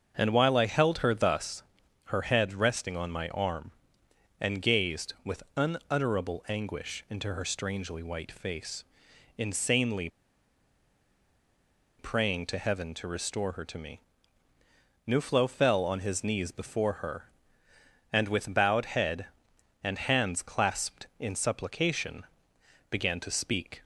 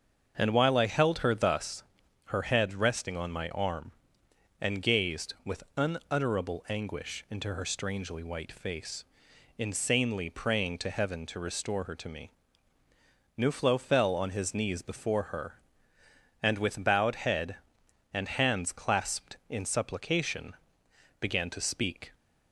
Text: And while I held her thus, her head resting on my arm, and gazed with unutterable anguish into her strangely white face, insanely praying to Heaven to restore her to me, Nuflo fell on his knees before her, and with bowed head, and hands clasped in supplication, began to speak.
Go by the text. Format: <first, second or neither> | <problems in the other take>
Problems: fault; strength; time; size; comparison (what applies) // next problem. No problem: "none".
second | starts louder than the rest; until 1.1 s; 7 dB; also in the second // pauses between "insanely" and "praying"; strong; at 10.0 s; 1.9 s long